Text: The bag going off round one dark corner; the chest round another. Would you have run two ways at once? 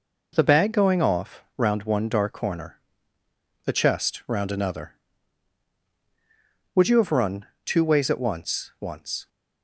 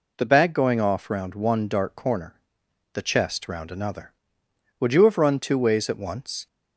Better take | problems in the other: second | pauses between "run" and "two"; slight; at 7.4 s; 0.18 s long // says "once" twice; at 8.7 s

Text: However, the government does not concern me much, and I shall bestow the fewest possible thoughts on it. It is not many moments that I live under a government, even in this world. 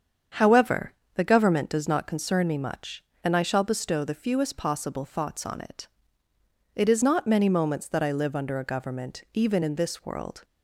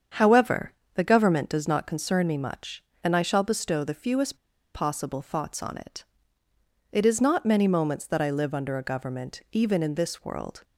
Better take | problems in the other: first | starts louder than the rest; strong; until 1.3 s; 7.5 dB; strong in the first // pauses between "fewest" and "possible"; at 4.3 s; 0.37 s long

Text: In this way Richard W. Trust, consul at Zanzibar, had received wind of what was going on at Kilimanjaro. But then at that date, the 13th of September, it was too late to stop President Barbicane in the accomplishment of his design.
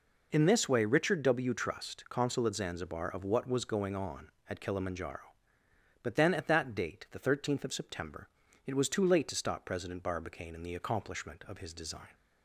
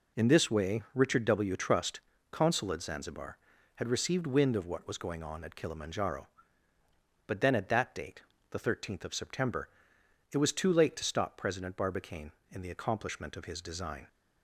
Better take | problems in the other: second | skips "had received wind"; at 3.0 s

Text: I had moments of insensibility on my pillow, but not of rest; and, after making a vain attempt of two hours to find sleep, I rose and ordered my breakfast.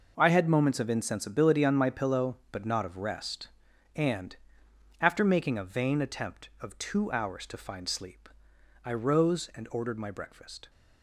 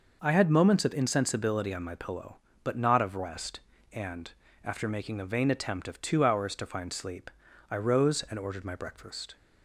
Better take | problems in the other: second | gets quieter; strong; throughout; 12 dB

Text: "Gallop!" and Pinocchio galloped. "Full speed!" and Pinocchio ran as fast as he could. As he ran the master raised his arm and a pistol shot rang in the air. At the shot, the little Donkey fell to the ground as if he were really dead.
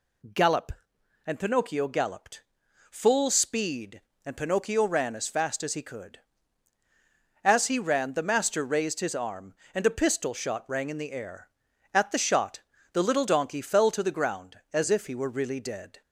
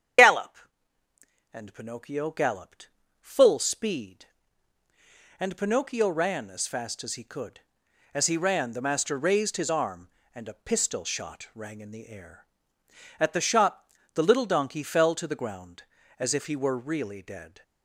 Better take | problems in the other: first | loses the start of "Gallop"; at 0.1 s; 65 ms // starts louder than the rest; strong; until 2.1 s; 9 dB

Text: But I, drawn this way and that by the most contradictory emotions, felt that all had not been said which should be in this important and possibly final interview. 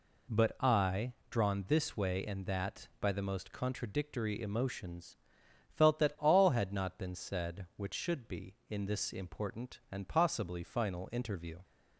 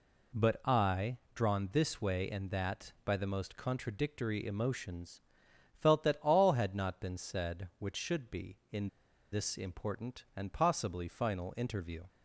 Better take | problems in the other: first | pauses between "in" and "this"; at 8.8 s; 0.44 s long

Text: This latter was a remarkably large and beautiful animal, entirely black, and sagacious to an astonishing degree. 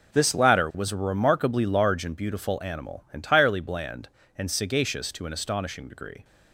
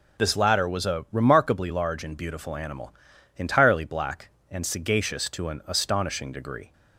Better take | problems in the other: second | says "bland" for "black"; at 3.5 s

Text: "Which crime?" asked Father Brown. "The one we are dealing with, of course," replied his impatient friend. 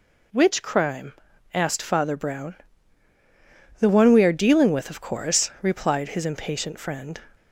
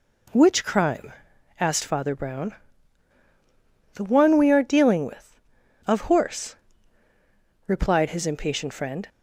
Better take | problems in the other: first | says "horse" for "course"; at 6.0 s

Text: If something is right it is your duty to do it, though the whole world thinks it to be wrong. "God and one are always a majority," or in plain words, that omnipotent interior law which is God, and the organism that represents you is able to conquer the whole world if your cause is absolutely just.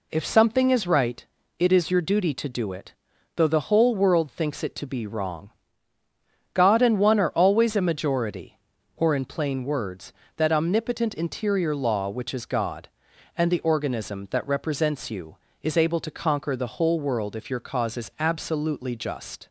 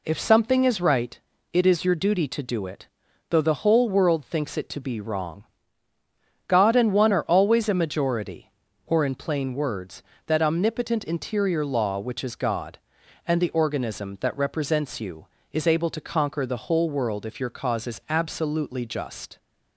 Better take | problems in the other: neither | pauses between "right" and "it"; slight; the same in both

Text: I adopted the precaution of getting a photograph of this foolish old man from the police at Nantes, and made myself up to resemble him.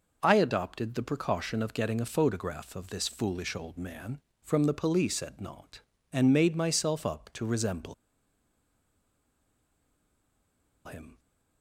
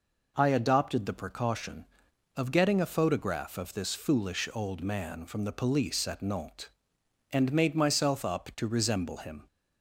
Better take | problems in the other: second | pauses between "resemble" and "him"; strong; at 7.9 s; 2.9 s long

